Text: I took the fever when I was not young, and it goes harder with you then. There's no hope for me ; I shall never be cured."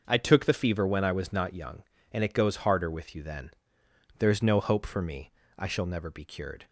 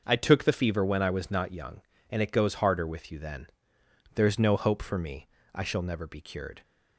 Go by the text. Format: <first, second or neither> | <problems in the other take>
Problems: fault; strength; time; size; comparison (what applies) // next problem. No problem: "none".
neither | starts louder than the rest; the same in both